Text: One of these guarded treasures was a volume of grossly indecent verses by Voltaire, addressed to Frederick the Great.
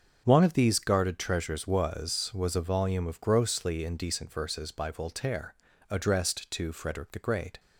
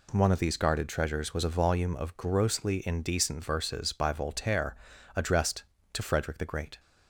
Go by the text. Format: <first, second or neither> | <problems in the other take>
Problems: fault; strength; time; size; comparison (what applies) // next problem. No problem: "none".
second | starts louder than the rest; until 1.2 s; 6.5 dB // says "was" twice; at 2.3 s